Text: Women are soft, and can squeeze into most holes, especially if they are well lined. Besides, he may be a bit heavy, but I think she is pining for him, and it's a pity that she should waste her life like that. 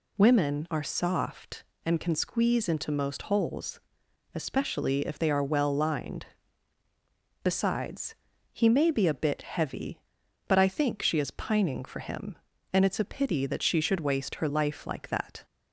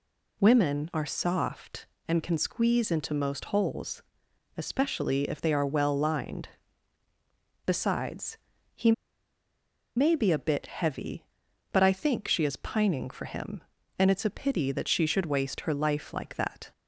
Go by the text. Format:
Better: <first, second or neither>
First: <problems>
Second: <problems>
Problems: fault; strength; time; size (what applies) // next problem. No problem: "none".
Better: first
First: none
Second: pauses between "he" and "may"; at 8.9 s; 1.0 s long